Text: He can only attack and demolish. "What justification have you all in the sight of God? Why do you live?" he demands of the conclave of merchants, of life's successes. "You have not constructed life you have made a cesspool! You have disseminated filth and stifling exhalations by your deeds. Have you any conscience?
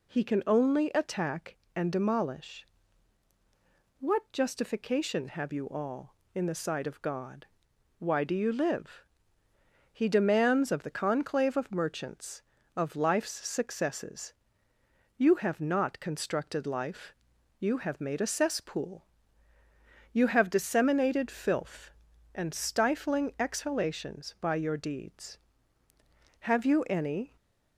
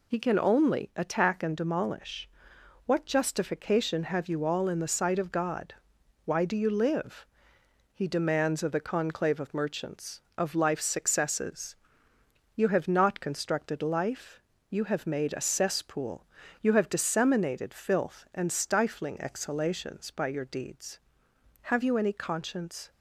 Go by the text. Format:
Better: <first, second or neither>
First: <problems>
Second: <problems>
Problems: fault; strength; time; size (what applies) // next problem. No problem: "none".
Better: second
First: pauses between "life" and "you"; noticeable; at 17.1 s; 0.46 s long // stays silent after the last word; slight; from 27.2 s on; 0.5 s long // stops before "conscience"; at 27.3 s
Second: pauses between "life" and "you"; slight; at 14.4 s; 0.26 s long